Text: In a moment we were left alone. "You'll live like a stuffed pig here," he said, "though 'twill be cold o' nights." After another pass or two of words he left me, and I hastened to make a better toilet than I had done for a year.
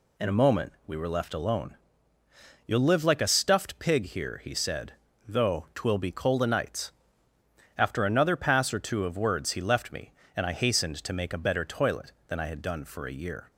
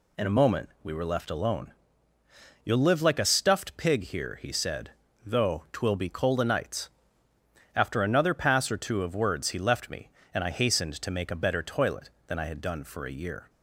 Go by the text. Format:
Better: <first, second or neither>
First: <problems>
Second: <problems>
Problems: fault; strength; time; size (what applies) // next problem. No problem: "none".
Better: neither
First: pauses between "moment" and "we"; slight; at 0.7 s; 0.16 s long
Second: pauses between "moment" and "we"; slight; at 0.6 s; 0.16 s long